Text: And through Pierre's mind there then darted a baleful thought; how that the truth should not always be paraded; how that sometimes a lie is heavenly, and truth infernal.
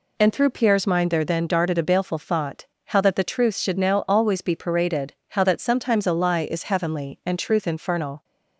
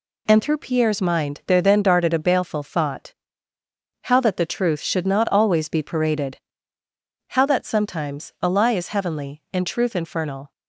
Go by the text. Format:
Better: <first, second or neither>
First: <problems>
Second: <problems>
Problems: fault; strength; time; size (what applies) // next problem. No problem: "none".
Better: second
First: says "now" for "not"; at 3.7 s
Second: none